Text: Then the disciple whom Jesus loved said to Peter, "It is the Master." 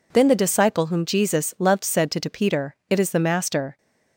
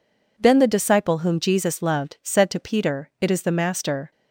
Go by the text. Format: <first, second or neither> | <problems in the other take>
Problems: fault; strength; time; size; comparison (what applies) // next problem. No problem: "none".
second | says "to" twice; at 2.1 s